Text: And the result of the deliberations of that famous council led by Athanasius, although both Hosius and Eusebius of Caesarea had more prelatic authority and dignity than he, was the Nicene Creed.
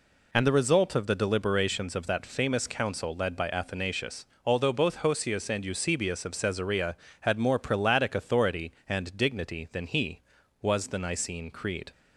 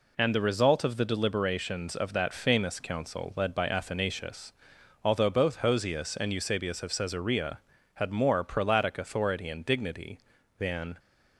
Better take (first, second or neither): first